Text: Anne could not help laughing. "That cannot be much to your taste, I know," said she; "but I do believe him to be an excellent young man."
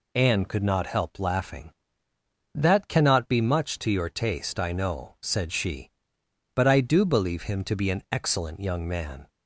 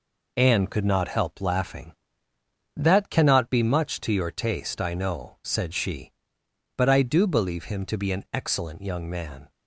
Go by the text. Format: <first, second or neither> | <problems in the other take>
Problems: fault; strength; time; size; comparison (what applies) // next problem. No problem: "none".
first | gets quieter; noticeable; throughout; 5 dB